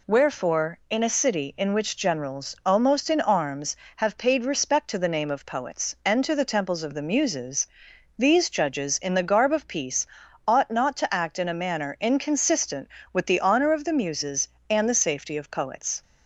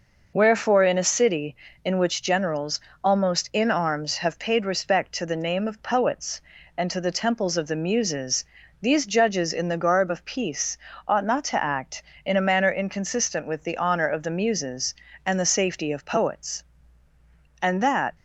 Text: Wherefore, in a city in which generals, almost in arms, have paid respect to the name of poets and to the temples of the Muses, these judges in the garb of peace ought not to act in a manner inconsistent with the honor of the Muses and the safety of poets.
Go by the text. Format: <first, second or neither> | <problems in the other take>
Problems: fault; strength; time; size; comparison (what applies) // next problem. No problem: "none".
first | pauses between "peace" and "ought"; slight; at 10.7 s; 0.32 s long; also in the first // goes on to say "And that"; from 17.6 s on; 0.54 s long